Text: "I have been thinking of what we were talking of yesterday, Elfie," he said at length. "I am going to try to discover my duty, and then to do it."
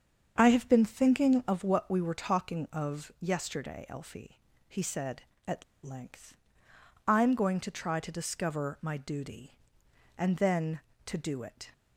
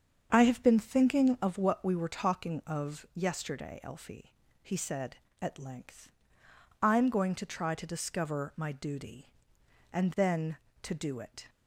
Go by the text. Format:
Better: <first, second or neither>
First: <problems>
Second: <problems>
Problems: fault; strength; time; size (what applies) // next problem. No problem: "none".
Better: second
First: starts louder than the rest; until 1.3 s; 7 dB // pauses between "at" and "length"; slight; at 5.6 s; 0.20 s long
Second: starts louder than the rest; strong; until 1.3 s; 7 dB